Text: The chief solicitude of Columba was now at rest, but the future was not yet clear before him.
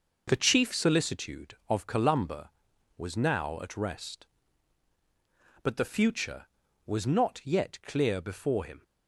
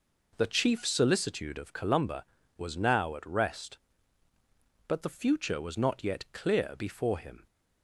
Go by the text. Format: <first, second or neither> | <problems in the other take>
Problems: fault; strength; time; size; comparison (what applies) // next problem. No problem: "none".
neither | none